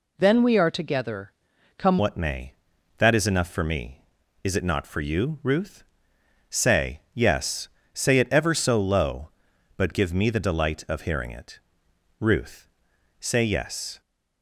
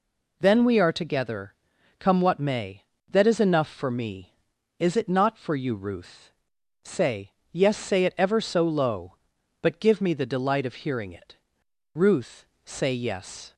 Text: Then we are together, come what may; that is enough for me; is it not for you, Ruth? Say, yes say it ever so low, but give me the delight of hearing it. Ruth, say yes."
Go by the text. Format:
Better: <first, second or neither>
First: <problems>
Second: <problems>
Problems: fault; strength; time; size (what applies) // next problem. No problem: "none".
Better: second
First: changes voice at "what"; from 1.9 s on; 12.1 s long // pauses between "yes" and "say"; slight; at 7.6 s; 0.24 s long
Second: none